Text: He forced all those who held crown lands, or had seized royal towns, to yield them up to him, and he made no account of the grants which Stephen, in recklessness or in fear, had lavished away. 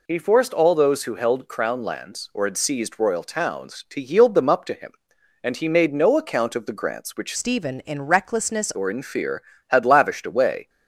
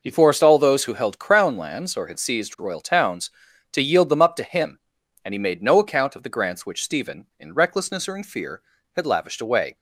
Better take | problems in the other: second | changes voice from "Stephen" to "recklessness"; from 7.3 to 8.7 s; 1.4 s long

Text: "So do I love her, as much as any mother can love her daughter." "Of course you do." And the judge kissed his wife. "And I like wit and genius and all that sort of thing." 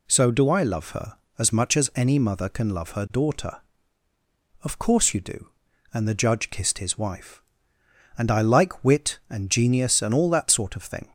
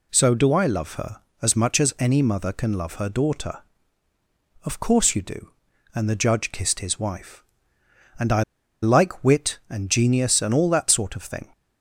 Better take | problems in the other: first | pauses between "I" and "like"; at 8.4 s; 0.40 s long

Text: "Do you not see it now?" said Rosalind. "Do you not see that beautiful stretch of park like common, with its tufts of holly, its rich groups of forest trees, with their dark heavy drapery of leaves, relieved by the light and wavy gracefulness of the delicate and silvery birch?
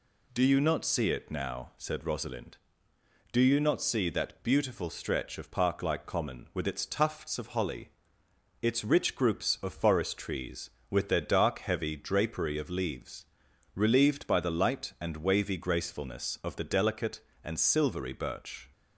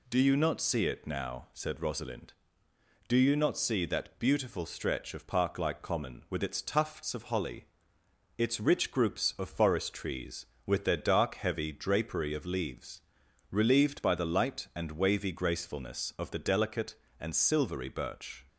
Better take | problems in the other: neither | none

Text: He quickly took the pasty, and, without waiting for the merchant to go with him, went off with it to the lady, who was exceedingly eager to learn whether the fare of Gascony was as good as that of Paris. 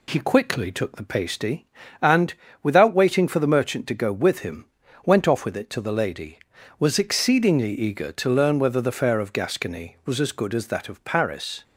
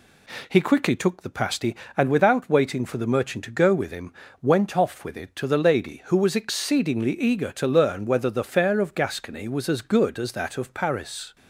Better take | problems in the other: second | skips "who"; at 6.5 s

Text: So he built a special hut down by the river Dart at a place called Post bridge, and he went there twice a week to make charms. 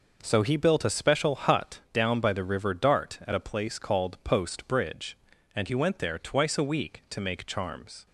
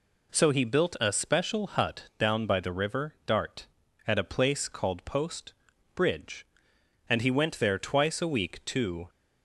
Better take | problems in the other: first | pauses between "Post" and "bridge"; at 5.5 s; 0.42 s long // stops before "make charms"; at 9.0 s

